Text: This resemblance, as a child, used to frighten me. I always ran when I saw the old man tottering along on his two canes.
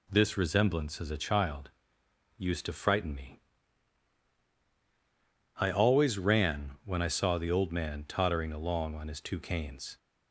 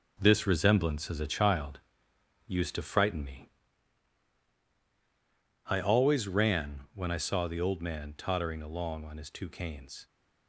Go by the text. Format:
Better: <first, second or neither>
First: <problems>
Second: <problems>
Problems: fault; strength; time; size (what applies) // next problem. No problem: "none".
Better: first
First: none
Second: gets quieter; strong; throughout; 7.5 dB